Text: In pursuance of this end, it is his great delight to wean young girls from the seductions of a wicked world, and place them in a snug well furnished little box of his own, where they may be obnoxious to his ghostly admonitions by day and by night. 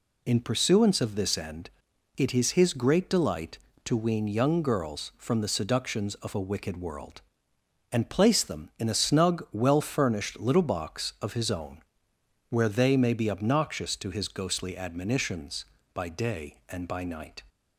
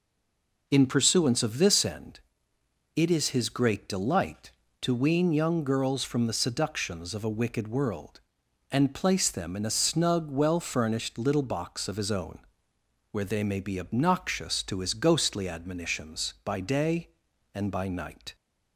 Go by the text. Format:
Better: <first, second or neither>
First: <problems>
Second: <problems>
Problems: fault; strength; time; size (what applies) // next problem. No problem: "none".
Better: first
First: none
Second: stays silent before the first word; slight; until 0.6 s; 0.6 s long